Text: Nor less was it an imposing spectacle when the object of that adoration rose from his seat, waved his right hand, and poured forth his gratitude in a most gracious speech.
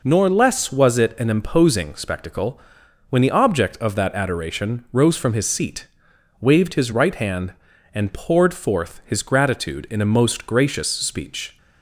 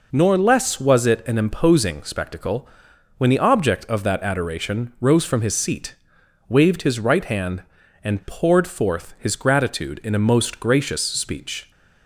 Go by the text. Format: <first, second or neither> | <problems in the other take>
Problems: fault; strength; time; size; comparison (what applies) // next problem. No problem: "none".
neither | pauses between "spectacle" and "when"; noticeable; the same in both